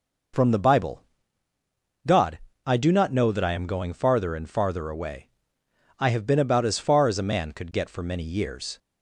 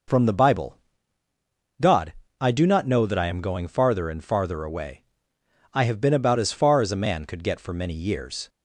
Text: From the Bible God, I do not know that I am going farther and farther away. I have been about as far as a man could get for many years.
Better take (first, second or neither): neither